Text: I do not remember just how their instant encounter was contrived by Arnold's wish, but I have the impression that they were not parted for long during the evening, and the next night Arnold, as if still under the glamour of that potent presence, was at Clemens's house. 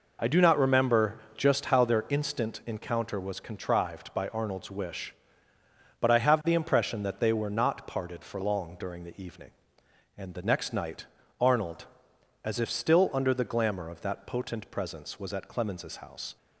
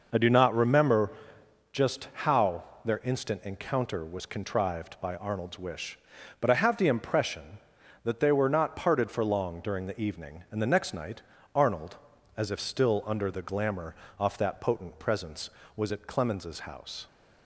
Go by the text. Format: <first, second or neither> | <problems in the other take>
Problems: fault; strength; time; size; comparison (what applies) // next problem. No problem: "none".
first | pauses between "remember" and "just"; noticeable; at 1.1 s; 0.62 s long; slight in the first // pauses between "how" and "their"; slight; at 2.6 s; 0.22 s long // pauses between "night" and "Arnold"; slight; at 11.2 s; 0.32 s long; slight in the first // says "off" for "of"; at 14.1 s